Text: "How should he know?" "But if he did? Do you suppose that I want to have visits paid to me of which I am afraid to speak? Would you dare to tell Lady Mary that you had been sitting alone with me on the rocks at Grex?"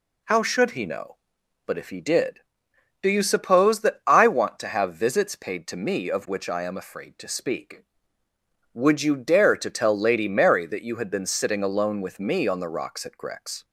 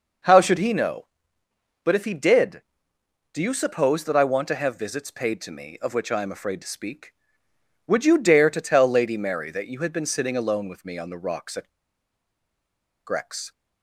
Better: first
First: none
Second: pauses between "at" and "Grex"; strong; at 11.6 s; 1.3 s long

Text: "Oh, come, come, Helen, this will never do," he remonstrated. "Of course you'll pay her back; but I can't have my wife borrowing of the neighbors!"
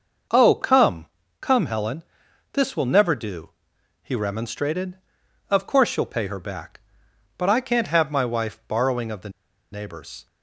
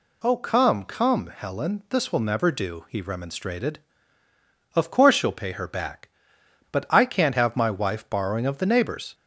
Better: second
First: starts louder than the rest; noticeable; until 1.6 s; 6 dB // pauses between "the" and "neighbors"; at 9.2 s; 0.42 s long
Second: none

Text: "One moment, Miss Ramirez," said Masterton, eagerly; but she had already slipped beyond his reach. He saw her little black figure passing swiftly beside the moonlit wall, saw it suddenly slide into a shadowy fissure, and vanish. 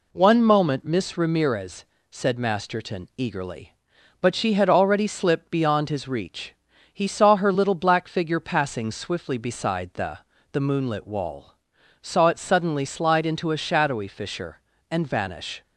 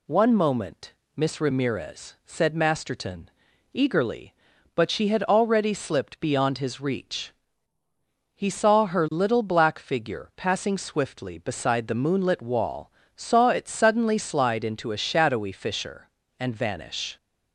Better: second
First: says "the" twice; at 10.5 s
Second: none

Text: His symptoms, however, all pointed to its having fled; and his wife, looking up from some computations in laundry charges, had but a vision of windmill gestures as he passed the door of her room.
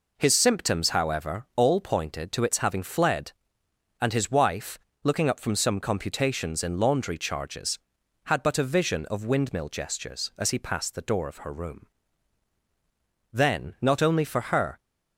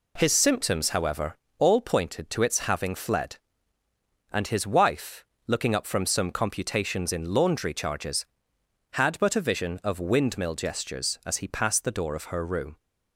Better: second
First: goes on to say "Then not only for her"; from 13.3 s on; 1.4 s long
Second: none

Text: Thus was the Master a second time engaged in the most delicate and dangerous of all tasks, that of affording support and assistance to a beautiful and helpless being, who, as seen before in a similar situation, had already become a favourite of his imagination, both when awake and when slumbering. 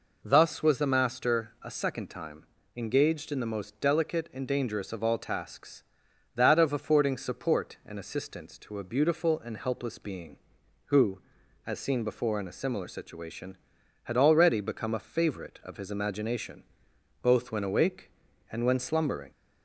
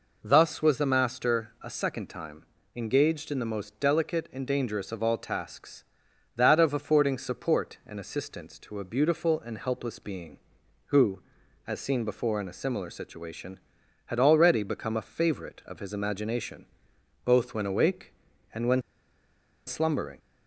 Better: first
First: pauses between "time" and "engaged"; slight; at 2.4 s; 0.30 s long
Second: pauses between "time" and "engaged"; slight; at 2.4 s; 0.30 s long // pauses between "when" and "slumbering"; noticeable; at 18.8 s; 0.85 s long

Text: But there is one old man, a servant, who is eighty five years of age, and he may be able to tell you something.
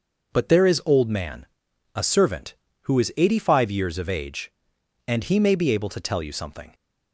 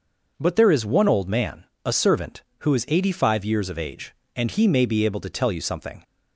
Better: second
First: skips "one"; at 0.8 s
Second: none

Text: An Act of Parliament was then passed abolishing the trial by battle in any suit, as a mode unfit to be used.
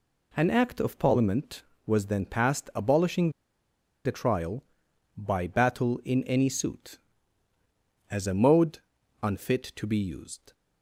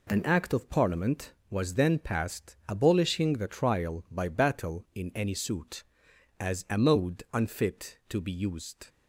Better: second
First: pauses between "abolishing" and "the"; noticeable; at 3.3 s; 0.74 s long // pauses between "mode" and "unfit"; at 8.7 s; 0.42 s long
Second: none

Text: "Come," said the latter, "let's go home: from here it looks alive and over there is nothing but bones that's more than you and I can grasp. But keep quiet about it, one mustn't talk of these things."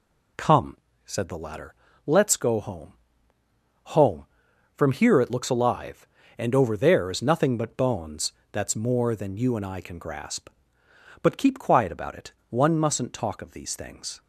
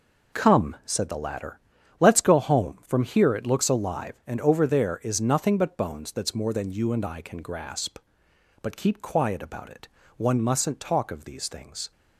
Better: second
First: says "home" twice; at 3.8 s // pauses between "bones" and "that's"; slight; at 8.3 s; 0.18 s long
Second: none

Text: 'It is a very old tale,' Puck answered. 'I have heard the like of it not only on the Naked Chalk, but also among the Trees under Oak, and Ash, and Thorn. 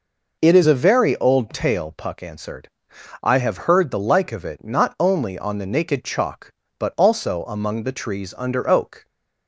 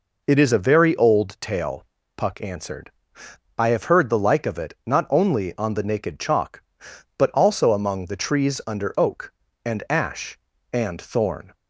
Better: second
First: stops before "and Ash and Thorn"; at 9.0 s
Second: none

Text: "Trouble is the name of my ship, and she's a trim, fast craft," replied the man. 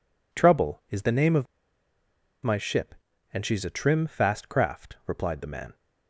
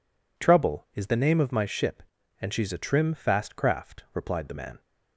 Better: second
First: pauses between "of" and "my"; noticeable; at 1.4 s; 0.96 s long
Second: none

